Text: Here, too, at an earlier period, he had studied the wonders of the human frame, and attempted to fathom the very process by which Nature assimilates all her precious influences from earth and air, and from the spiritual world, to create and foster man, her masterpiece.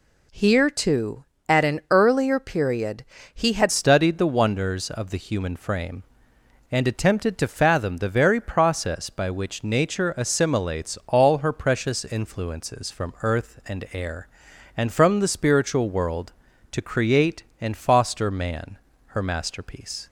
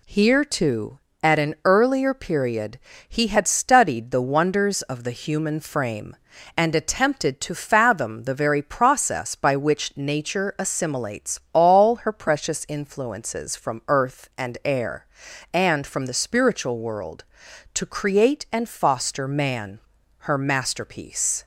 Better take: second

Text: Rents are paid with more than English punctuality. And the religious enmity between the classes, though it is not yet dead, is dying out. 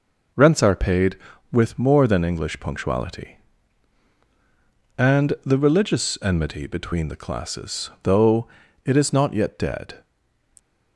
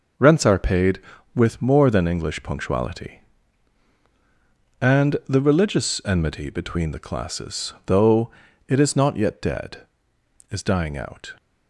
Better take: second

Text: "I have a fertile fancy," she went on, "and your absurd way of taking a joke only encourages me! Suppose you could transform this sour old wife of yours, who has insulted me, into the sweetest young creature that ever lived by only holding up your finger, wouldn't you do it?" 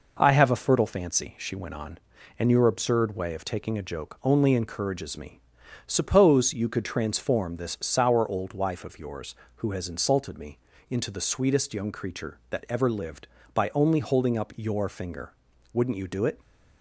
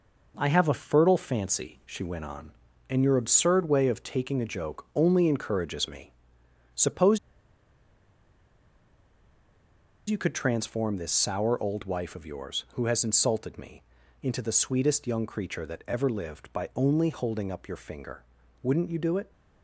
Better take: first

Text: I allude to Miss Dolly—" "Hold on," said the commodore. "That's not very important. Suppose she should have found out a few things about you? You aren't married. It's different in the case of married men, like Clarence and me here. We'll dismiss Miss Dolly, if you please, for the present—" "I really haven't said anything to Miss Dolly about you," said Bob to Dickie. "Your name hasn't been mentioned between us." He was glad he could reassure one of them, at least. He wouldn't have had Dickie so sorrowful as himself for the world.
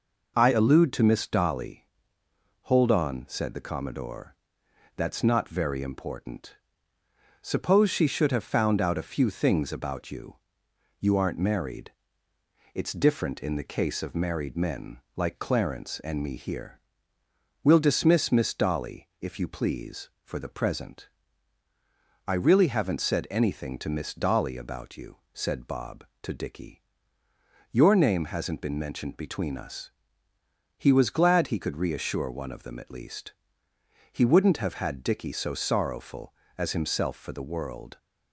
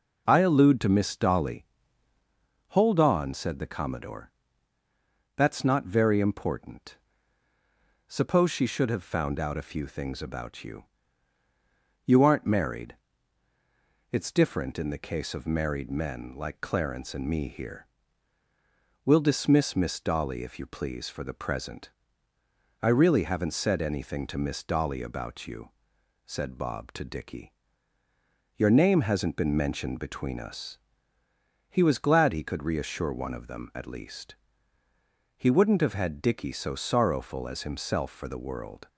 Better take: neither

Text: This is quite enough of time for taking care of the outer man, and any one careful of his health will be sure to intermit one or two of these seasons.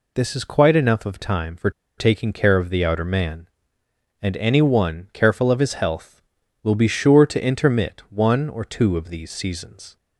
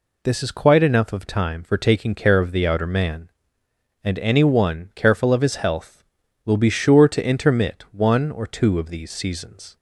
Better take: second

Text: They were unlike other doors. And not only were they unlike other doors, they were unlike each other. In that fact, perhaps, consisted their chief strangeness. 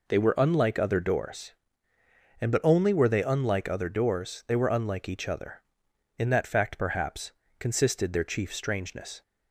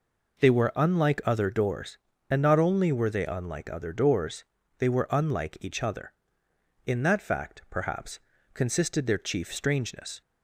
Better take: second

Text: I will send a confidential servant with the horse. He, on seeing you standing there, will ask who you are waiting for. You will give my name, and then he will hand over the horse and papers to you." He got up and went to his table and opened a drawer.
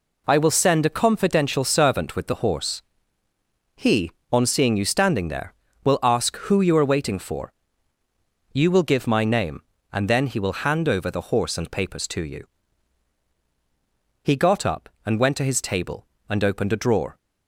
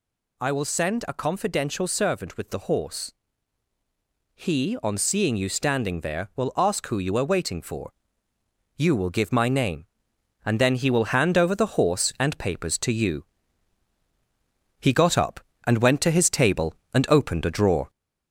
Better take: first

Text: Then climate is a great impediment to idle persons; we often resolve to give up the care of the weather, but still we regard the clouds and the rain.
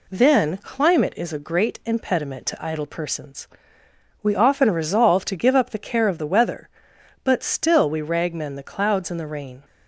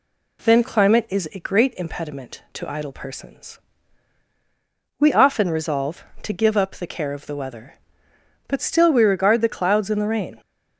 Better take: second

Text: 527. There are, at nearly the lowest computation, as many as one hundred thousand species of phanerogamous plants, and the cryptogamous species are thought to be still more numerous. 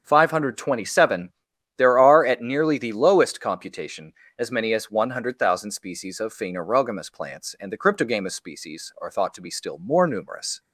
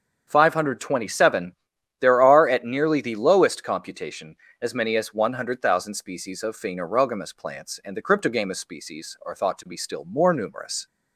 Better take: neither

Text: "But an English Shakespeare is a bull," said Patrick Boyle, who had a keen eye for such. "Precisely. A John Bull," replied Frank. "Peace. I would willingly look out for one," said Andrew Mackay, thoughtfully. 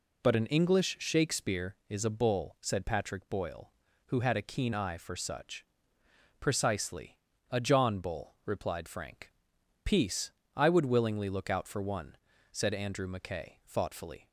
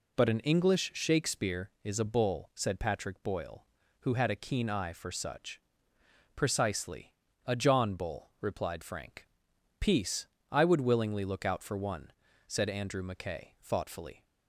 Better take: neither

